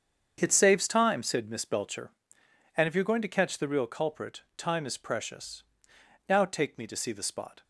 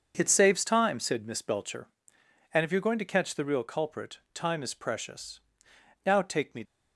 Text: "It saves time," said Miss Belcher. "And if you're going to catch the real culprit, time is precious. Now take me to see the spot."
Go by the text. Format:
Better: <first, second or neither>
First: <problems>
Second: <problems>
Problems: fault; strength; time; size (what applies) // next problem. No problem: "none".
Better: first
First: starts louder than the rest; strong; until 1.4 s; 7.5 dB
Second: starts louder than the rest; until 1.1 s; 6.5 dB // stops before "to see the spot"; at 6.6 s